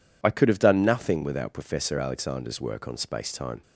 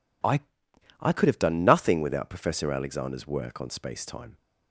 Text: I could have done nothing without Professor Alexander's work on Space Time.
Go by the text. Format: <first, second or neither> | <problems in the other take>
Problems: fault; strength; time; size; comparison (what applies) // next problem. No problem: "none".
first | says "I" twice; at 1.0 s